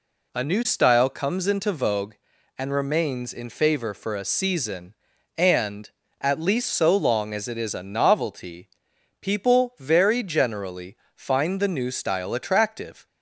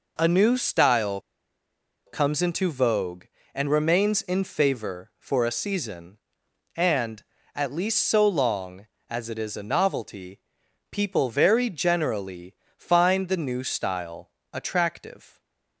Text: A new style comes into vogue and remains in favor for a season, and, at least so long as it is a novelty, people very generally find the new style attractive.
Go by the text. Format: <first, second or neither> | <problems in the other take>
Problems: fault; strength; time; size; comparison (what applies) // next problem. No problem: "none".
first | pauses between "style" and "comes"; noticeable; at 1.1 s; 0.87 s long // pauses between "generally" and "find"; slight; at 12.5 s; 0.24 s long; slight in the first // pauses between "style" and "attractive"; slight; at 14.3 s; 0.22 s long